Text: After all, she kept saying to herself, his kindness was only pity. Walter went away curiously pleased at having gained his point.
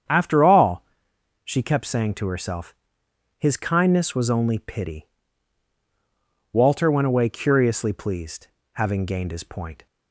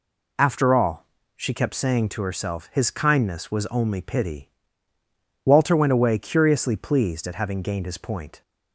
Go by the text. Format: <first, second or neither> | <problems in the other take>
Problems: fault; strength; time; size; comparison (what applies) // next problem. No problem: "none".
second | starts louder than the rest; strong; until 1.6 s; 8 dB // skips "at"; at 8.6 s